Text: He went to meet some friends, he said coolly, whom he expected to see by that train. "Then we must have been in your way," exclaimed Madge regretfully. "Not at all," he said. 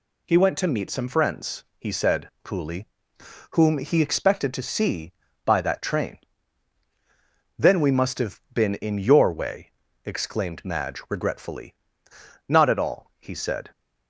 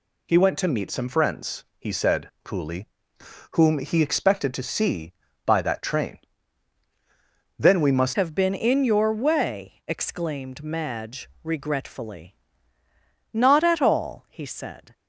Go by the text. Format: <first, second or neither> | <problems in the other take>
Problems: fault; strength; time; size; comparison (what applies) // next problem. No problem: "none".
first | changes voice at "have"; from 8.1 s on; 6.8 s long